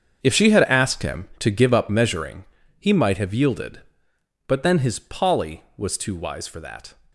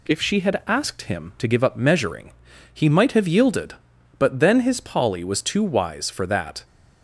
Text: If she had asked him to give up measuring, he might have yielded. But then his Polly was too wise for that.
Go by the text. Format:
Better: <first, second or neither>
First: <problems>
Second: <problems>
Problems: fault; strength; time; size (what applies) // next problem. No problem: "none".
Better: second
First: gets quieter; strong; throughout; 13.5 dB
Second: none